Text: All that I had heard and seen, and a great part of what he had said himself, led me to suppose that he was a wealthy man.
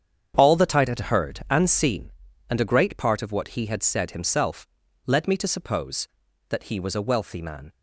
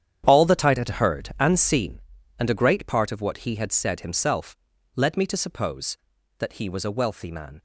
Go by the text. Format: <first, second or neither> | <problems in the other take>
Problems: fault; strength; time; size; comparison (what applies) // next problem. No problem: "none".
first | gets quieter; strong; throughout; 13.5 dB // starts louder than the rest; strong; until 1.2 s; 9.5 dB; strong in the first